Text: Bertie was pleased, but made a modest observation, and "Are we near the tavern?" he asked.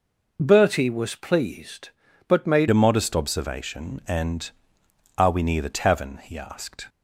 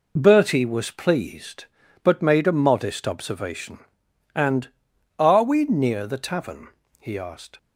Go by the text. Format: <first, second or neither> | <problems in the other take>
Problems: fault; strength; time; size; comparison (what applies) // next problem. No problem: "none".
second | changes voice at "a"; from 2.6 s on; 4.2 s long